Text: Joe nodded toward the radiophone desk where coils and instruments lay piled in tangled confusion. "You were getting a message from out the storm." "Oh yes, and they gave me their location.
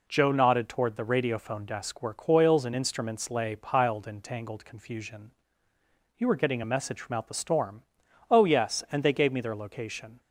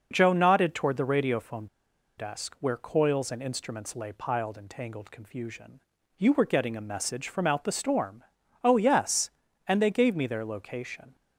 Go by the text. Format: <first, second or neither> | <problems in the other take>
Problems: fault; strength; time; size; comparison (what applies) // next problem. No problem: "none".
first | pauses between "radiophone" and "desk"; noticeable; at 1.6 s; 0.52 s long